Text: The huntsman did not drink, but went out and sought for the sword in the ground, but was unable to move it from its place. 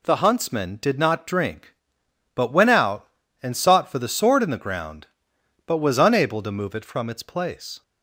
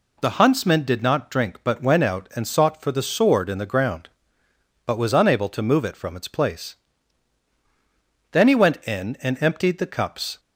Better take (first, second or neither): first